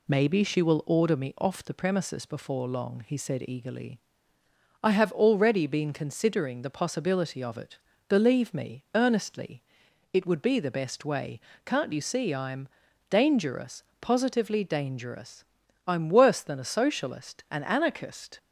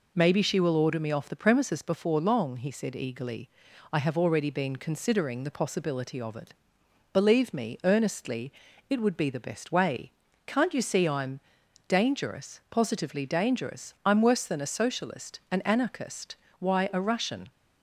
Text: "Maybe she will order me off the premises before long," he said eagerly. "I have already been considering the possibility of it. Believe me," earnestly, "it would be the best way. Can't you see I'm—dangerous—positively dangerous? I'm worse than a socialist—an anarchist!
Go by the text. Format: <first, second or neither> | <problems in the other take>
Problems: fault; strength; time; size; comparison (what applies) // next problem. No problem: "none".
first | goes on to say "Why a Russian"; noticeable; from 16.5 s on; 0.92 s long